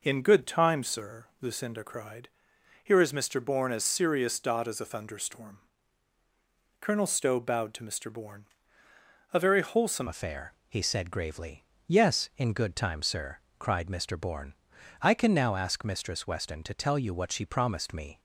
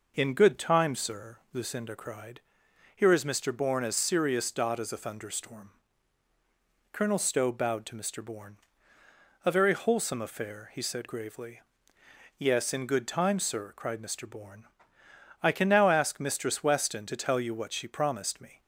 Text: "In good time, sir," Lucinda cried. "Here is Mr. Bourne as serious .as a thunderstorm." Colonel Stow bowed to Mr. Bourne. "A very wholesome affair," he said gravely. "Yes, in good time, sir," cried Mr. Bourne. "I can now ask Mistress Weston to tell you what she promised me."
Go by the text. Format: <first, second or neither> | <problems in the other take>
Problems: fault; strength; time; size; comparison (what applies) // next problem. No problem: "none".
second | changes voice at "affair"; from 10.0 s on; 8.1 s long